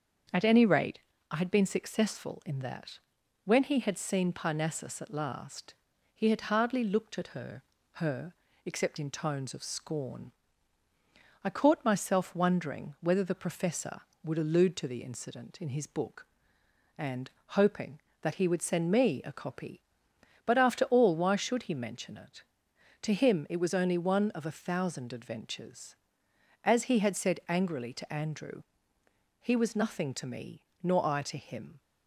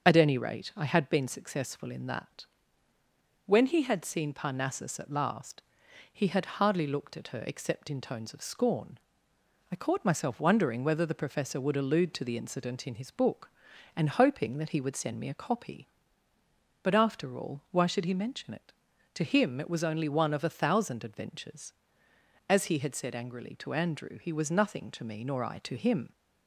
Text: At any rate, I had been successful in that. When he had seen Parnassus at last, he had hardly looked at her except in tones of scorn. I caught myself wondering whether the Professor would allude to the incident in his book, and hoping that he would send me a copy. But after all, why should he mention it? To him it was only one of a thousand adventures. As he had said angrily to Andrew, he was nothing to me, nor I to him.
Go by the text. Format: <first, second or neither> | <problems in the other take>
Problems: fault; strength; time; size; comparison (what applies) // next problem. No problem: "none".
second | starts louder than the rest; until 1.6 s; 7 dB; also in the second // says "her" twice; at 7.9 s // pauses between "and" and "hoping"; slight; at 17.3 s; 0.18 s long